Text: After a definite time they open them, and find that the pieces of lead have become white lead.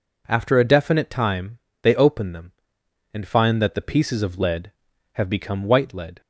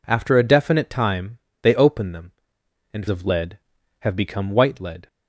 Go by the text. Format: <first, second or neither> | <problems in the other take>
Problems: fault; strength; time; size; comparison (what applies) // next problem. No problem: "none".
first | pauses between "time" and "they"; slight; at 1.3 s; 0.24 s long; slight in the first // skips "find that the pieces"; at 3.0 s